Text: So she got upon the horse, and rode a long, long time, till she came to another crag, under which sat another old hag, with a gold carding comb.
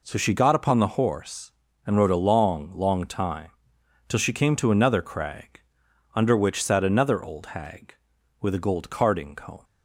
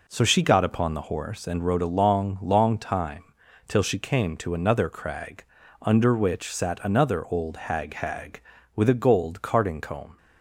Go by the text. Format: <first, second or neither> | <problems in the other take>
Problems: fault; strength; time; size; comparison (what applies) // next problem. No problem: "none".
first | says "hag" twice; at 7.9 s